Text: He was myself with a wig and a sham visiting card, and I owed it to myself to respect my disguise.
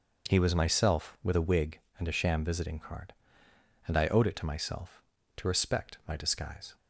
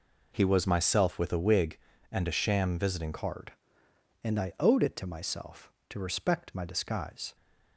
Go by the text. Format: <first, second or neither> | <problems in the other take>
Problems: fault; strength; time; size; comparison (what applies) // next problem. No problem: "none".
first | changes voice at "card"; from 3.1 s on; 4.2 s long